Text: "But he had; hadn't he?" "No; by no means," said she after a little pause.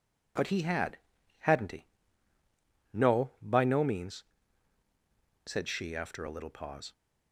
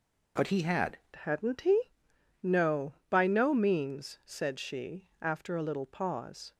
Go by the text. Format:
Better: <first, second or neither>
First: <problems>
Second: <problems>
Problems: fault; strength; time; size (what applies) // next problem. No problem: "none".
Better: first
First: none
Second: changes voice at "hadn't"; from 1.1 s on; 5.4 s long